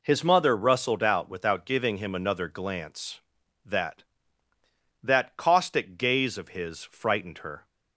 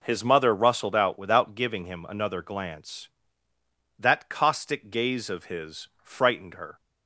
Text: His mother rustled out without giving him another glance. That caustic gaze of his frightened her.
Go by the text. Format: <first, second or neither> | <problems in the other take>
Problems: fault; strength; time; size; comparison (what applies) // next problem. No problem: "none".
second | says "That" twice; at 5.0 s